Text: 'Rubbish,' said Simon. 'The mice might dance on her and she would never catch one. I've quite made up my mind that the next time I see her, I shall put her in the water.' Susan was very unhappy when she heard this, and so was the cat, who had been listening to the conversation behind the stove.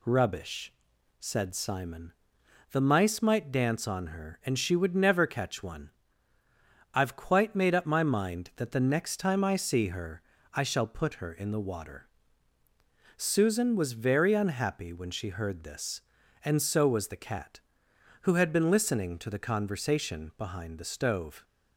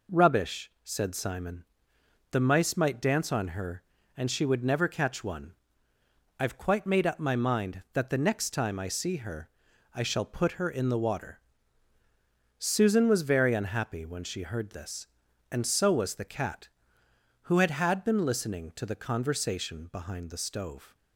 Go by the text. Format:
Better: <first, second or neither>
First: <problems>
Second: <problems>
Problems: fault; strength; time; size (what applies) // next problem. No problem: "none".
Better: first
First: none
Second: says "had" twice; at 17.7 s